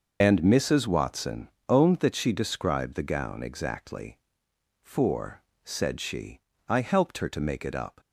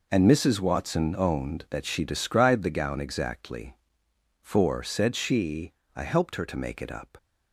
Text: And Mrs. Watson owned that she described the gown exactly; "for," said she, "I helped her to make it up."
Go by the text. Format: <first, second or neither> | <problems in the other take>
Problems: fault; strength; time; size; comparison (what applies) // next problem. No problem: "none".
second | loses the start of "And"; at 0.2 s; 50 ms // pauses between "Watson" and "owned"; slight; at 1.4 s; 0.18 s long